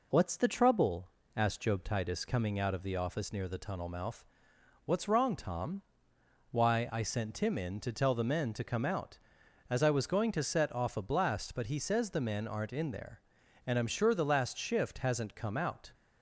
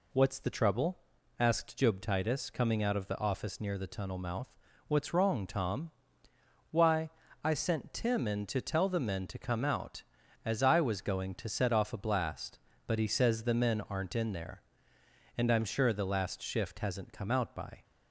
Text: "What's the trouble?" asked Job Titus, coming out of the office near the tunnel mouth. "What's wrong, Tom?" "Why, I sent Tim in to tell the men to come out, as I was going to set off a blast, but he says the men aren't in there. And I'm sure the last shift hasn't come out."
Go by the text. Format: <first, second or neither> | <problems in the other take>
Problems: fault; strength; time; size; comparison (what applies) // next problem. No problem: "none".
first | goes on to say "By"; slight; from 17.5 s on; 0.28 s long